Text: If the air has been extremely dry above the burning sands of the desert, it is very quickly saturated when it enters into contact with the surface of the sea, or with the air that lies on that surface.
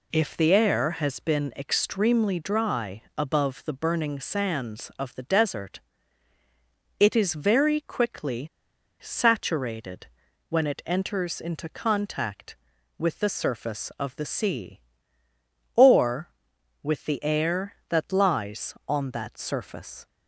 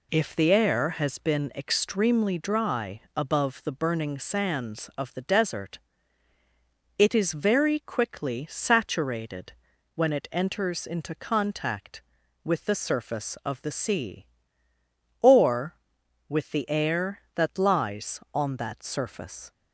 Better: second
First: pauses between "quickly" and "saturated"; noticeable; at 8.4 s; 0.54 s long // pauses between "saturated" and "when"; at 10.0 s; 0.44 s long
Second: pauses between "saturated" and "when"; at 9.5 s; 0.44 s long

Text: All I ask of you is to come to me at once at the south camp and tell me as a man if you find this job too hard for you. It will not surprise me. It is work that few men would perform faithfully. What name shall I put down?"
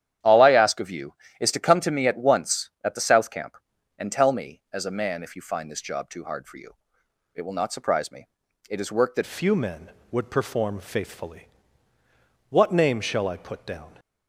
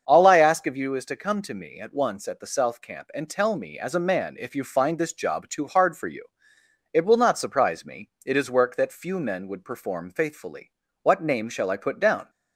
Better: second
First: starts louder than the rest; strong; until 1.4 s; 10 dB // changes voice at "few"; from 9.2 s on; 4.7 s long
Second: starts louder than the rest; until 1.0 s; 7 dB

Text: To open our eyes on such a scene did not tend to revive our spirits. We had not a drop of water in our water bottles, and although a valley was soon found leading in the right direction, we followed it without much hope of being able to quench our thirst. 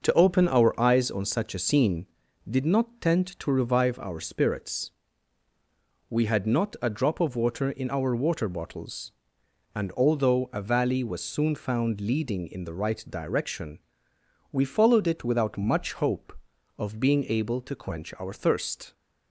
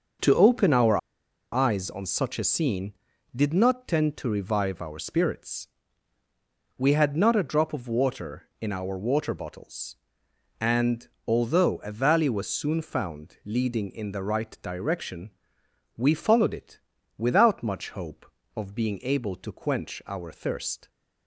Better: first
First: none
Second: starts louder than the rest; until 1.7 s; 6 dB // pauses between "our" and "eyes"; noticeable; at 0.9 s; 0.54 s long // pauses between "and" and "although"; slight; at 11.0 s; 0.22 s long // pauses between "it" and "without"; at 16.7 s; 0.38 s long

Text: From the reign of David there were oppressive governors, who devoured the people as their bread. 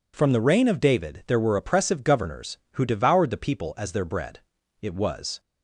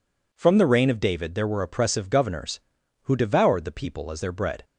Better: second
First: goes on to say "It was"; from 4.8 s on; 0.58 s long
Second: none

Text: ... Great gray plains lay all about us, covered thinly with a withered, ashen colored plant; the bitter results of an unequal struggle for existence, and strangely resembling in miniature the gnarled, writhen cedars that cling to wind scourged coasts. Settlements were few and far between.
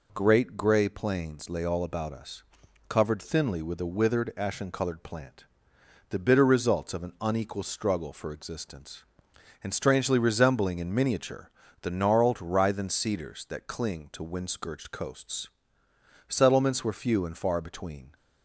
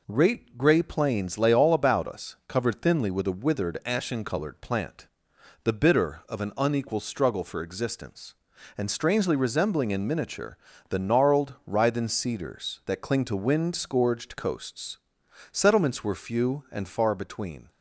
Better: first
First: pauses between "miniature" and "the"; slight; at 11.4 s; 0.34 s long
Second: skips "results"; at 6.2 s // pauses between "miniature" and "the"; slight; at 10.5 s; 0.32 s long

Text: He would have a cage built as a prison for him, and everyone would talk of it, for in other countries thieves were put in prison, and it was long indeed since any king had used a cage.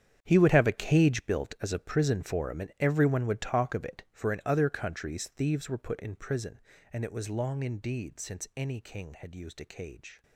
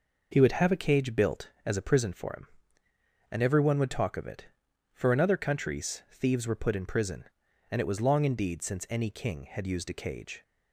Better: second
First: gets quieter; strong; throughout; 15 dB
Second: none

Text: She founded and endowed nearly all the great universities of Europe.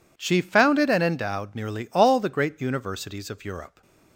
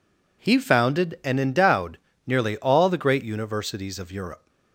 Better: first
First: none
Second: says "He" for "She"; at 0.4 s // pauses between "endowed" and "nearly"; slight; at 1.9 s; 0.28 s long

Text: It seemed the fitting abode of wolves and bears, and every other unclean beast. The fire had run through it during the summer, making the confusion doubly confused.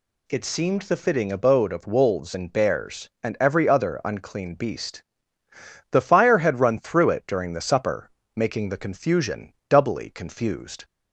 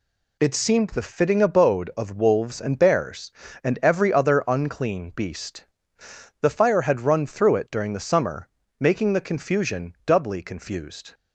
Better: second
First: says "supper" for "summer"; at 7.6 s // pauses between "confusion" and "doubly"; slight; at 9.5 s; 0.16 s long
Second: none

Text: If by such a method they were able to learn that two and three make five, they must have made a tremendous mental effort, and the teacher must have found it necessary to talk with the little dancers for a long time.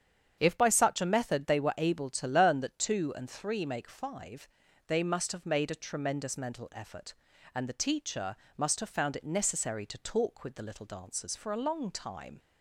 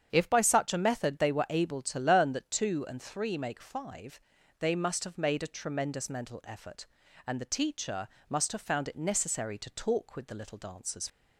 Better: first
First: starts louder than the rest; strong; until 1.3 s; 8 dB // pauses between "teacher" and "must"; slight; at 8.3 s; 0.20 s long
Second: starts louder than the rest; strong; until 1.1 s; 8.5 dB // pauses between "teacher" and "must"; slight; at 8.0 s; 0.20 s long // stops before "for a long time"; at 11.0 s

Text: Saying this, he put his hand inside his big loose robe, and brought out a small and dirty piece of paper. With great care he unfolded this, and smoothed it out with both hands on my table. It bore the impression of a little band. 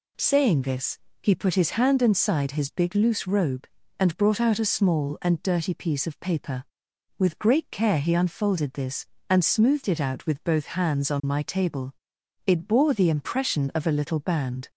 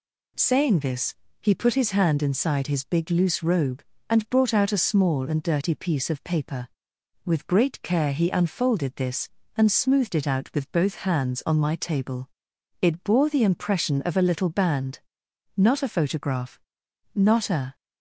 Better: first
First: none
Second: goes on to say "Not a photograph Not a"; strong; from 15.5 s on; 2.2 s long

